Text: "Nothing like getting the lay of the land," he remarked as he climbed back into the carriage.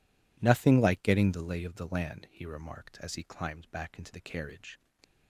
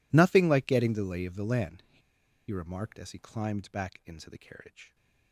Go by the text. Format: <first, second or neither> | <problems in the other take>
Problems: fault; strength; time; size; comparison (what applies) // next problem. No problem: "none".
first | pauses between "he" and "remarked"; noticeable; at 2.0 s; 0.50 s long